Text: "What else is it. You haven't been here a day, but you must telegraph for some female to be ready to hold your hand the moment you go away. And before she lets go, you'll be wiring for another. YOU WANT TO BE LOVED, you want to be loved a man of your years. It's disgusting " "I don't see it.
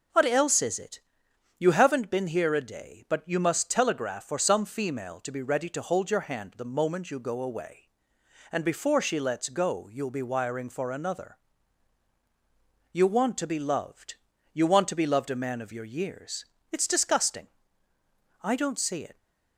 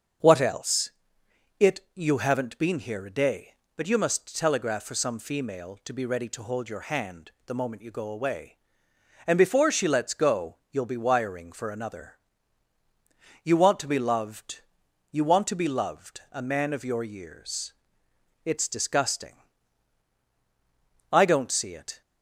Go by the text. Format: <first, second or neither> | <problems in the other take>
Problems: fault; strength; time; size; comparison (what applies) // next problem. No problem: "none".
first | starts louder than the rest; until 2.0 s; 6.5 dB // skips "is"; at 1.2 s // pauses between "hand" and "the"; slight; at 7.3 s; 0.16 s long